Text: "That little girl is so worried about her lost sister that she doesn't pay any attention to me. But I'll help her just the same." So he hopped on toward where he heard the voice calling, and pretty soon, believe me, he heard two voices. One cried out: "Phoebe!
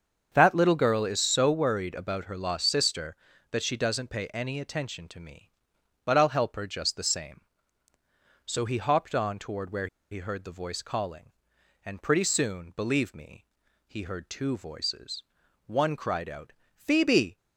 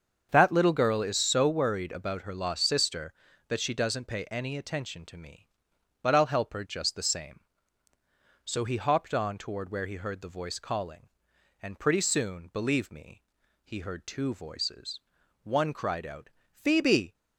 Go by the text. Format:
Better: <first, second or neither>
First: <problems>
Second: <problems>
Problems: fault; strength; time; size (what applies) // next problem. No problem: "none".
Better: second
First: starts louder than the rest; until 1.3 s; 7 dB // pauses between "where" and "he"; slight; at 9.8 s; 0.24 s long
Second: starts louder than the rest; until 1.3 s; 7 dB